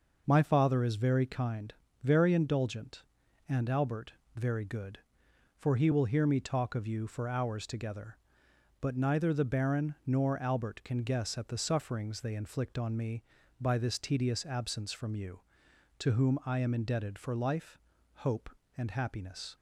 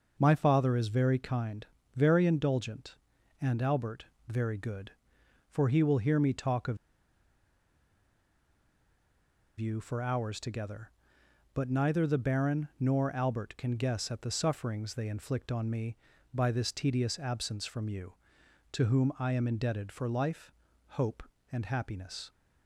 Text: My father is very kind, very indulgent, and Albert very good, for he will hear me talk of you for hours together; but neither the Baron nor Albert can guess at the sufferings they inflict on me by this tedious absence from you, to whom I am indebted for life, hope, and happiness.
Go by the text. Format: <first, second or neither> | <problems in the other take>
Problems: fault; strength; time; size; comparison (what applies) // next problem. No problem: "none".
first | pauses between "Albert" and "very"; slight; at 4.0 s; 0.22 s long; slight in the first // pauses between "of" and "you"; strong; at 6.7 s; 2.8 s long